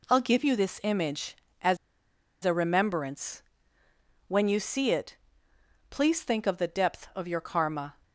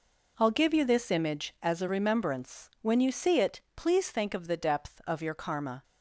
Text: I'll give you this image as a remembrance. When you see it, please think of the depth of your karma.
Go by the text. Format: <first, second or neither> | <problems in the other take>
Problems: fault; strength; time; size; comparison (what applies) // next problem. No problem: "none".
second | pauses between "as" and "a"; noticeable; at 1.7 s; 0.67 s long